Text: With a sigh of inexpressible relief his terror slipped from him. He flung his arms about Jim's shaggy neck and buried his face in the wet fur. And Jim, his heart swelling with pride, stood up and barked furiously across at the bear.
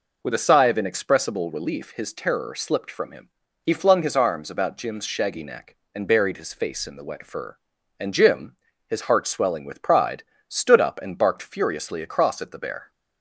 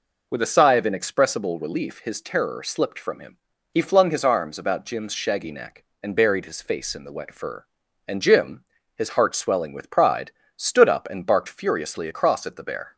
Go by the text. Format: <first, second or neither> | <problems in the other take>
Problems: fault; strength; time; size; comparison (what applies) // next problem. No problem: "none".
neither | none